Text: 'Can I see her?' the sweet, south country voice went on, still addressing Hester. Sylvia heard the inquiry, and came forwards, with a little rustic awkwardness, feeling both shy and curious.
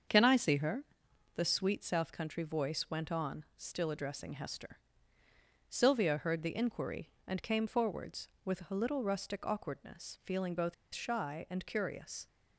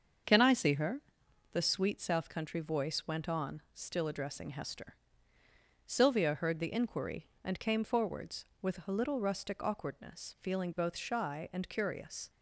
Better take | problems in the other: second | starts louder than the rest; until 1.6 s; 7 dB; also in the second // pauses between "both" and "shy"; slight; at 10.7 s; 0.20 s long

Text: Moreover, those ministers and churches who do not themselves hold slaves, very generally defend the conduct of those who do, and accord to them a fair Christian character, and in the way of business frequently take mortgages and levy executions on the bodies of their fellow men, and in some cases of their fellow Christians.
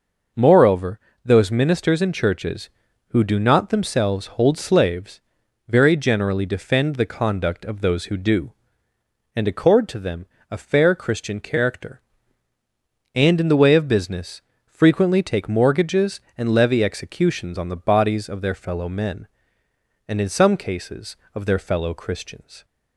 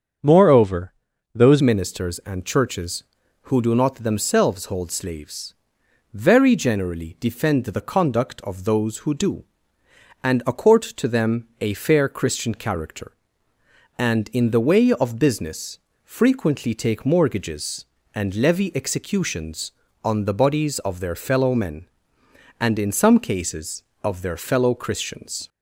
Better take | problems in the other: first | starts louder than the rest; until 1.6 s; 7 dB // changes voice at "ministers"; from 1.6 s on; 23.8 s long // pauses between "them" and "a"; slight; at 11.4 s; 0.16 s long; slight in the first // pauses between "business" and "frequently"; slight; at 15.7 s; 0.26 s long; slight in the first

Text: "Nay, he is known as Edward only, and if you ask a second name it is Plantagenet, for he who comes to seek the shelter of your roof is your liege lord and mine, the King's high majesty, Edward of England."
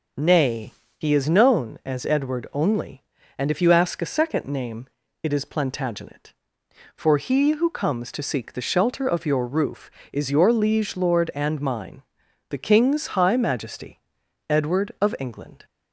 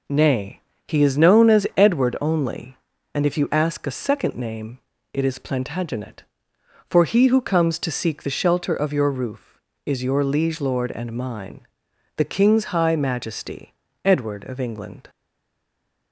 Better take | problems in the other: first | pauses between "name" and "it"; slight; at 4.7 s; 0.36 s long; slight in the first // stays silent after the last word; from 15.0 s on; 1.1 s long

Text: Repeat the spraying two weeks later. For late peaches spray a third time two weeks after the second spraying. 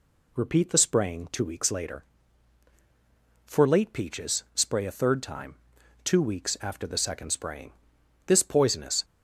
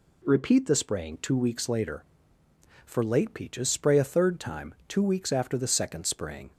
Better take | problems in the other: second | pauses between "time" and "two"; noticeable; at 5.5 s; 0.48 s long // goes on to say "This poisonous"; noticeable; from 8.2 s on; 0.78 s long

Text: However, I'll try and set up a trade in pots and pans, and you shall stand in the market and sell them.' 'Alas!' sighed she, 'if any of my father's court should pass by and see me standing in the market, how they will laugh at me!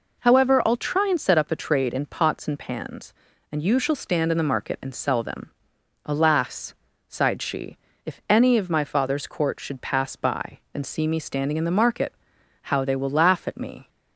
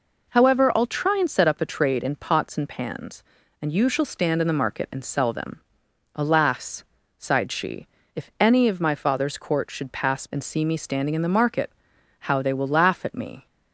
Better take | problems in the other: first | skips "by"; at 10.2 s

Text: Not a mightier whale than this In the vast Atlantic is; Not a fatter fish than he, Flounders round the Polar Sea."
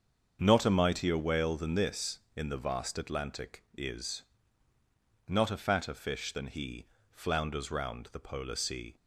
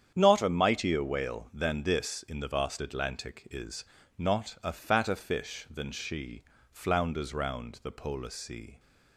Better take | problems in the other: first | starts louder than the rest; strong; until 1.1 s; 8.5 dB; also in the first // says "she" for "he"; at 5.9 s

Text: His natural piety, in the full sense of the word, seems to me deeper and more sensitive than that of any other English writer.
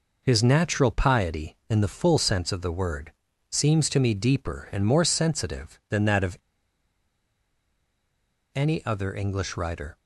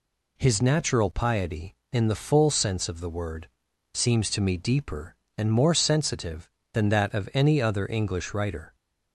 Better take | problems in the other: second | pauses between "of" and "any"; strong; at 6.3 s; 2.1 s long

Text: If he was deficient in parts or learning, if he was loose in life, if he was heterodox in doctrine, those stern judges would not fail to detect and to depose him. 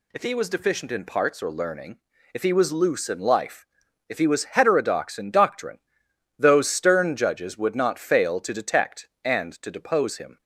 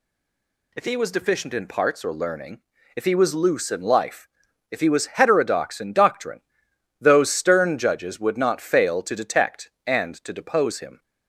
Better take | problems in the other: first | stays silent before the first word; slight; until 0.7 s; 0.7 s long

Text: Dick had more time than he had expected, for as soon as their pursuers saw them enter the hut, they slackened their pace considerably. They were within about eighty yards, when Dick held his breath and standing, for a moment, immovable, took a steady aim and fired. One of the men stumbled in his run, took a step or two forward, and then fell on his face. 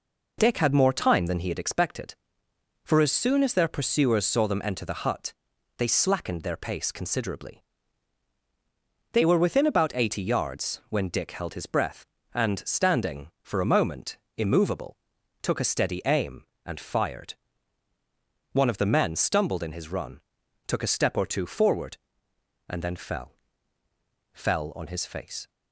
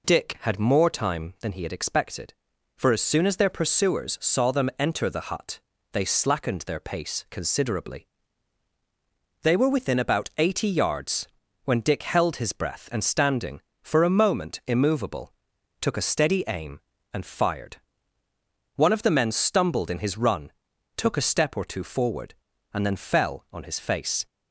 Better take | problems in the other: second | says "fell" twice; at 24.3 s

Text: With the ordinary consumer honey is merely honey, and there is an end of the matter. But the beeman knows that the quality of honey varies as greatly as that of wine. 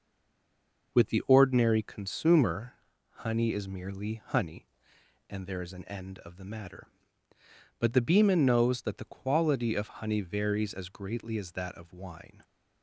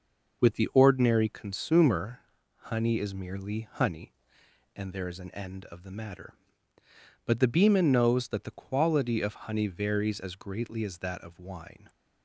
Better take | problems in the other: second | stays silent before the first word; slight; until 0.9 s; 0.9 s long // pauses between "consumer" and "honey"; at 2.7 s; 0.38 s long; also in the second

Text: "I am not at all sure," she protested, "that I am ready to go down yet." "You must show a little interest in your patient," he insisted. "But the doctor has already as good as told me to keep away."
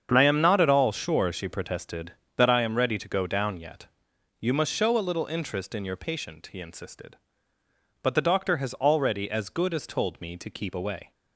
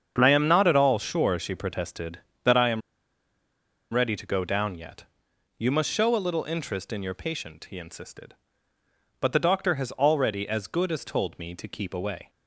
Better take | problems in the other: first | starts louder than the rest; strong; until 1.1 s; 7.5 dB; strong in the first // pauses between "am" and "ready"; at 2.8 s; 1.1 s long

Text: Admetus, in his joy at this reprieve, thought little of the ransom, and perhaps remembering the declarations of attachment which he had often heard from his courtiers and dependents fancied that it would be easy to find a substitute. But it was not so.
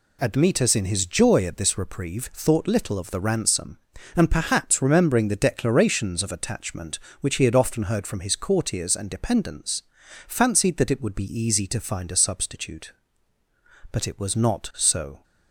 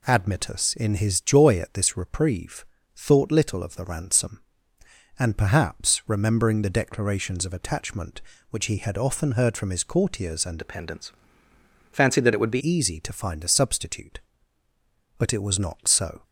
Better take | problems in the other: first | changes voice from "dependents" to "be"; from 10.5 to 12.6 s; 2.1 s long // pauses between "dependents" and "fancied"; noticeable; at 11.1 s; 0.78 s long; also in the first

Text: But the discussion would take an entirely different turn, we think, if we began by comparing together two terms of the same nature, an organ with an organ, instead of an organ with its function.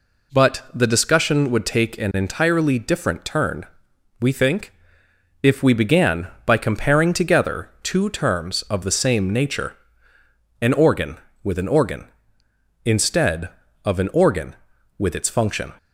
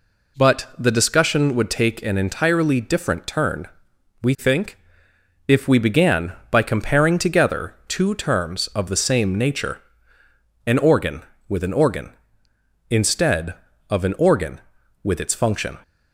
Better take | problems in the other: neither | none

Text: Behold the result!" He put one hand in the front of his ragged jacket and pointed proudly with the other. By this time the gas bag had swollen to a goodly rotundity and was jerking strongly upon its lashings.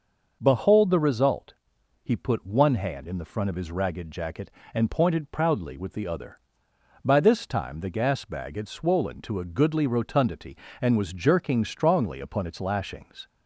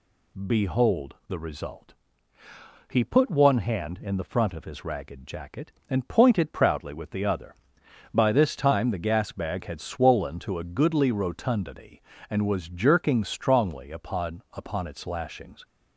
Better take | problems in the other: first | says "upon" twice; at 14.5 s

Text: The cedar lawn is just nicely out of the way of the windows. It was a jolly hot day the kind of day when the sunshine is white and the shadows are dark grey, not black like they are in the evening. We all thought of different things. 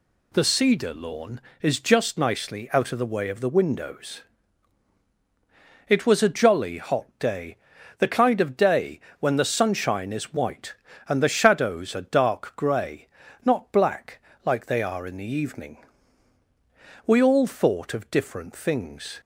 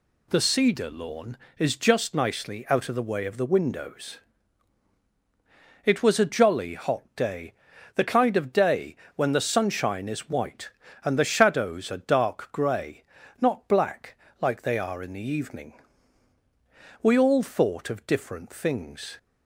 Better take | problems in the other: neither | pauses between "day" and "the"; the same in both // pauses between "day" and "when"; slight; the same in both // pauses between "black" and "like"; slight; the same in both

